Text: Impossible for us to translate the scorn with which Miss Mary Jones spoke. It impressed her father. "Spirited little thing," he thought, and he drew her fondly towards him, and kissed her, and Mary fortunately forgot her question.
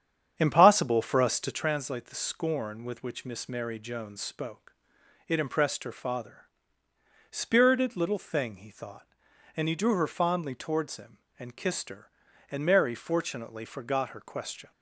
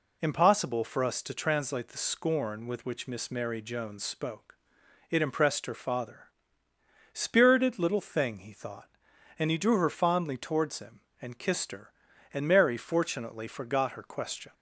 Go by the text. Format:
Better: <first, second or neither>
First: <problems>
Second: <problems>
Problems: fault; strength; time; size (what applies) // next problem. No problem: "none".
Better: second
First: starts louder than the rest; strong; until 1.6 s; 8.5 dB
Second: none